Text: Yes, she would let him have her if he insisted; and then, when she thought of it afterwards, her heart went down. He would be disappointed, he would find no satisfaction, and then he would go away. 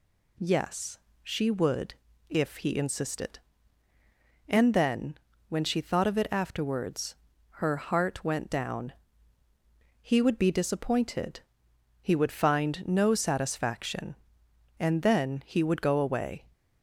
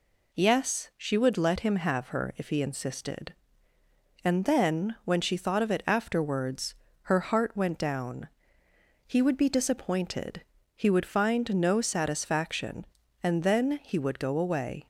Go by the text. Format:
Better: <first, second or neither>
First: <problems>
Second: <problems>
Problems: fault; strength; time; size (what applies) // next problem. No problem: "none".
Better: second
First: skips "let him have her"; at 2.1 s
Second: none